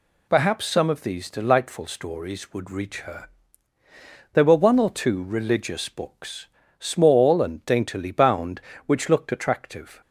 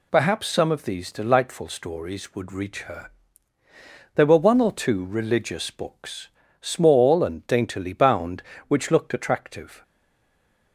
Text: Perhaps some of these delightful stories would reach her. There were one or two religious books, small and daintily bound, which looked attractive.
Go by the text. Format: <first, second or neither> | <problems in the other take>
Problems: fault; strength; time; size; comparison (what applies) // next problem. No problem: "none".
first | stays silent after the last word; slight; from 9.8 s on; 0.9 s long